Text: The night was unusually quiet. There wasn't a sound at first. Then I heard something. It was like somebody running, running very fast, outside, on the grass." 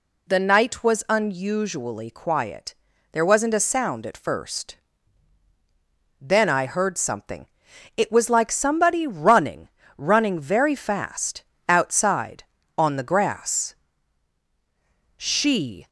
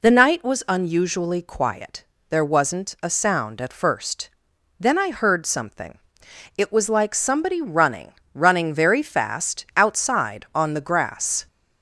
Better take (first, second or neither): second